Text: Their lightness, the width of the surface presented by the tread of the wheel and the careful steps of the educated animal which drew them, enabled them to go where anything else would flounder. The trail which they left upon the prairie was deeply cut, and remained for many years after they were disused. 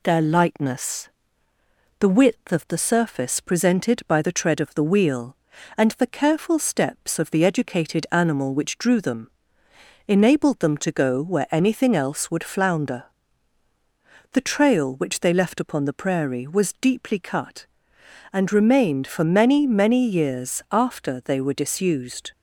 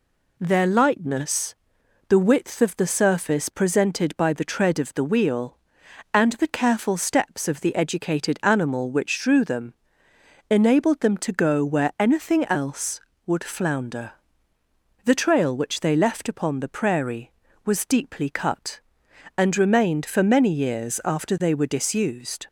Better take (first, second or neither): second